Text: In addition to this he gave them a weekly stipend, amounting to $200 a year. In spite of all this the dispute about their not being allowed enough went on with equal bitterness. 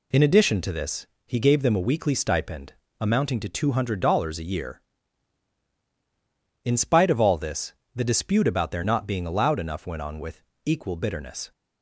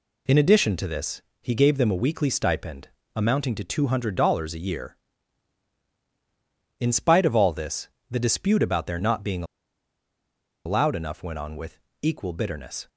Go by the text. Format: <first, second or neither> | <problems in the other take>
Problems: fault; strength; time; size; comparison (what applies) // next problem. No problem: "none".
first | pauses between "this" and "he"; slight; at 1.2 s; 0.20 s long; slight in the first // pauses between "this" and "the"; slight; at 7.8 s; 0.24 s long; slight in the first // pauses between "being" and "allowed"; at 9.4 s; 1.2 s long // pauses between "with" and "equal"; slight; at 11.7 s; 0.24 s long; slight in the first